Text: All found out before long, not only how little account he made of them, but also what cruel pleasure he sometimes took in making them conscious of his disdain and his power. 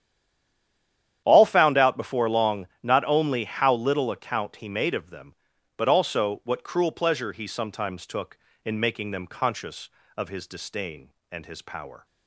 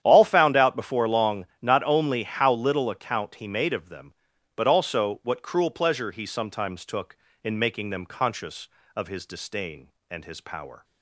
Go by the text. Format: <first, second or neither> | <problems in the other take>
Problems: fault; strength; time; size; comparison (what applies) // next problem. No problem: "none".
second | stays silent before the first word; noticeable; until 1.2 s; 1.2 s long // starts louder than the rest; strong; until 2.2 s; 10 dB; strong in the second